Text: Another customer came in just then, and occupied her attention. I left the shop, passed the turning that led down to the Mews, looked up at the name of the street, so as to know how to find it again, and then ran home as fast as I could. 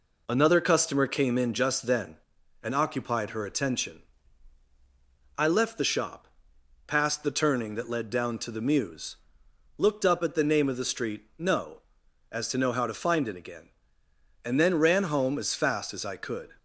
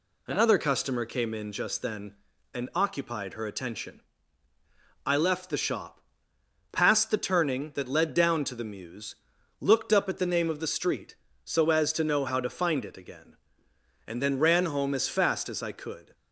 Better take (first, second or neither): second